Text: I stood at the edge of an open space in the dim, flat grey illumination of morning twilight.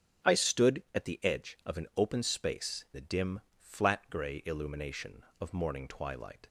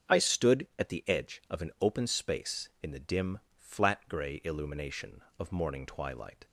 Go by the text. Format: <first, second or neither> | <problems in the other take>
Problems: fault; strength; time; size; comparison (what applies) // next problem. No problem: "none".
second | starts louder than the rest; until 1.3 s; 7 dB; also in the second // skips "in"; at 2.8 s